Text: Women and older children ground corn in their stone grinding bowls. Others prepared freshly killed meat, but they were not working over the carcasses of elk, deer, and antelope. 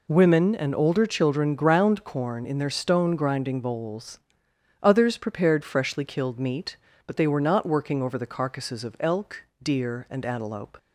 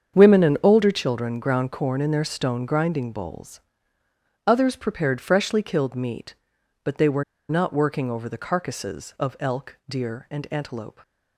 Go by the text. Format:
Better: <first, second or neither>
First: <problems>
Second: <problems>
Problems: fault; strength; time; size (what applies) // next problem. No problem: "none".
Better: first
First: none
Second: starts louder than the rest; strong; until 1.2 s; 7.5 dB // pauses between "were" and "not"; slight; at 7.2 s; 0.26 s long